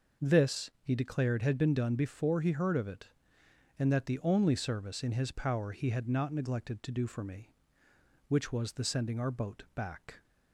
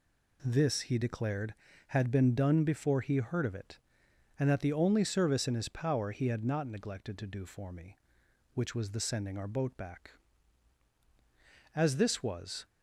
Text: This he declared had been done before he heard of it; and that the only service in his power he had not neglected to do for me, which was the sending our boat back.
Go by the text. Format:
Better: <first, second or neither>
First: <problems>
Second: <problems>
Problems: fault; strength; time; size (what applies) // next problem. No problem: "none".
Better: first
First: none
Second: goes on to say "As this was"; noticeable; from 11.7 s on; 0.90 s long